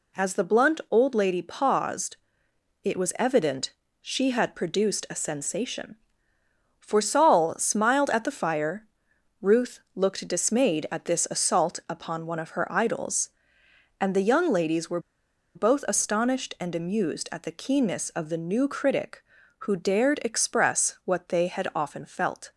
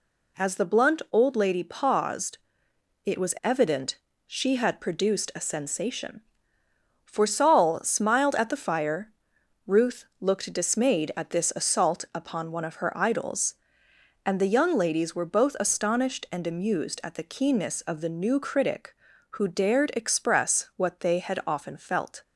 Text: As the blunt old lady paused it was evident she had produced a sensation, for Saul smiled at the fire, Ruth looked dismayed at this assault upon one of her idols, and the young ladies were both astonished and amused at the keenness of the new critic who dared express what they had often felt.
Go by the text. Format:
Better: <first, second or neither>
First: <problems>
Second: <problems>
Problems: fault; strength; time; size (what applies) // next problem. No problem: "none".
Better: second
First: pauses between "paused" and "it"; noticeable; at 2.1 s; 0.66 s long // pauses between "evident" and "she"; slight; at 3.7 s; 0.28 s long // pauses between "Ruth" and "looked"; slight; at 9.7 s; 0.16 s long // pauses between "were" and "both"; noticeable; at 14.9 s; 0.56 s long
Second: pauses between "paused" and "it"; noticeable; at 2.3 s; 0.66 s long // pauses between "evident" and "she"; slight; at 3.9 s; 0.28 s long // pauses between "Ruth" and "looked"; slight; at 10.0 s; 0.16 s long